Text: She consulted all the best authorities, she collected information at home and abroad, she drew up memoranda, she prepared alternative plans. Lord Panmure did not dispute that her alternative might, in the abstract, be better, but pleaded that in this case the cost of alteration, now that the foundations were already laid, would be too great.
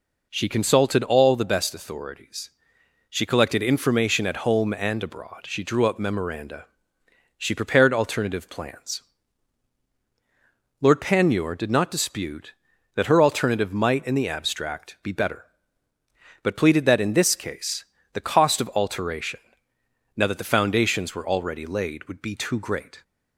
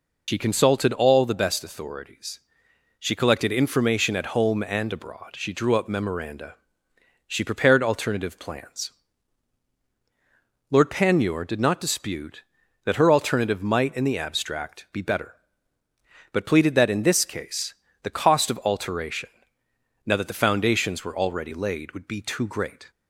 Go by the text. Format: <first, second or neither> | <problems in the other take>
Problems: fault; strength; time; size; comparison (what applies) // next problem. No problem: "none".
first | loses the start of "She"; at 0.2 s; 80 ms // pauses between "case" and "the"; slight; at 17.7 s; 0.28 s long; slight in the first